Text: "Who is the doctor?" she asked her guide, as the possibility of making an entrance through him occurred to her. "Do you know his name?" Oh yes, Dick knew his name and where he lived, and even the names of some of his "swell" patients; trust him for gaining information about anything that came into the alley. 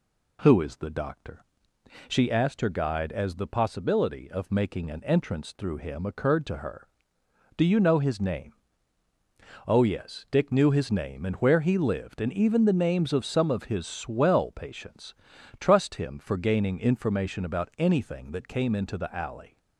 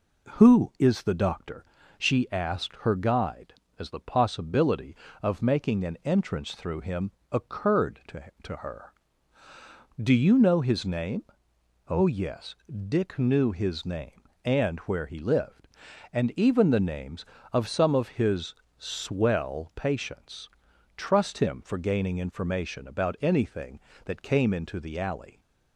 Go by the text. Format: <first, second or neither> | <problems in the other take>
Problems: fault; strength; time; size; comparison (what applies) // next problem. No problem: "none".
first | pauses between "him" and "occurred"; slight; at 7.1 s; 0.22 s long // says "to" twice; at 8.4 s // pauses between "his" and "swell"; slight; at 18.5 s; 0.24 s long